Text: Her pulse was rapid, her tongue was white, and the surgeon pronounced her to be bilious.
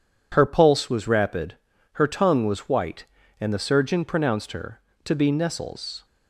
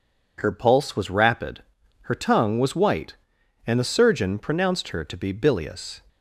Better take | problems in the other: second | says "nestles" for "bilious"; at 5.3 s

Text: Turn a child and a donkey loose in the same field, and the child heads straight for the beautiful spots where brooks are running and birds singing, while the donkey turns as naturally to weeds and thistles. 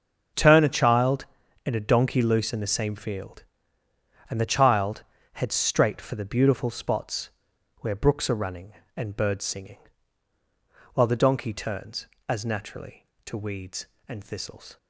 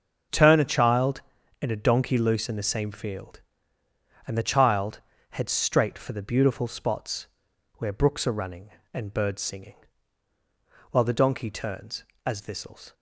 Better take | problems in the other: first | starts louder than the rest; until 1.6 s; 6.5 dB; also in the first // pauses between "child" and "heads"; slight; at 5.0 s; 0.30 s long; slight in the first // pauses between "spots" and "where"; noticeable; at 7.2 s; 0.52 s long; noticeable in the first // skips "naturally to weeds and"; at 12.3 s

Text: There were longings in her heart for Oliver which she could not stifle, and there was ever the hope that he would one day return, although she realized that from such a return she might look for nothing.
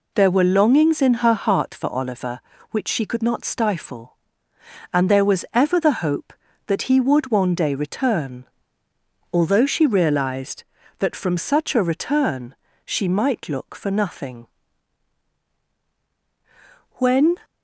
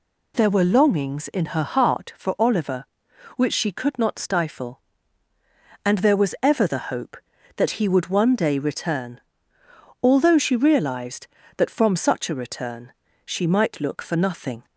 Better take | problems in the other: second | pauses between "return" and "she"; slight; at 12.5 s; 0.30 s long; slight in the second // goes on to say "When"; slight; from 16.9 s on; 0.40 s long

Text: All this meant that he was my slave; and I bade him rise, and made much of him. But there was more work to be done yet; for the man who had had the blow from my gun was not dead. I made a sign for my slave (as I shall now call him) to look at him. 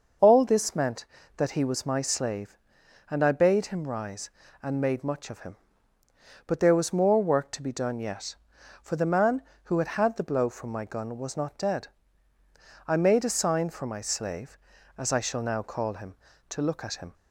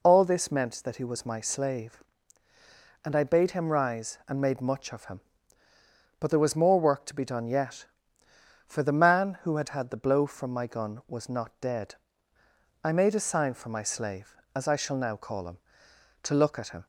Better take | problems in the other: neither | none

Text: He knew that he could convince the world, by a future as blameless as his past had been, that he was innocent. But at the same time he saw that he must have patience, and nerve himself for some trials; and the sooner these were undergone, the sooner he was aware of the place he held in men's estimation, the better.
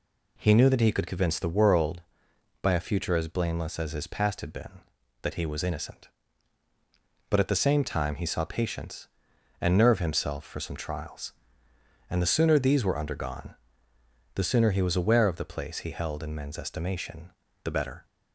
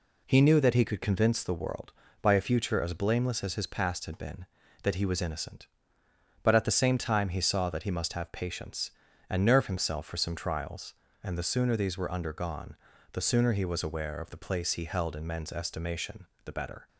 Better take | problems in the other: second | skips "that he must have"; at 8.4 s

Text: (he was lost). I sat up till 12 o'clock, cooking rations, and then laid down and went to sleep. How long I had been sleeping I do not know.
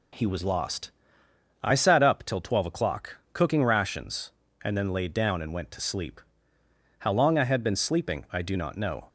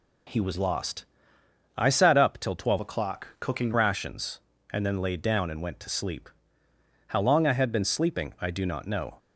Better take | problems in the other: first | changes voice from "o'clock" to "cooking"; from 2.8 to 3.7 s; 0.9 s long

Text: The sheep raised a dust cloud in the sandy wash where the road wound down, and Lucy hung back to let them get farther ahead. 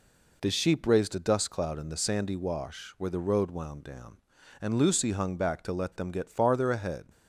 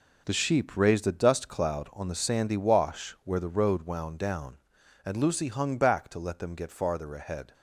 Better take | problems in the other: first | says "on" for "in"; at 1.9 s

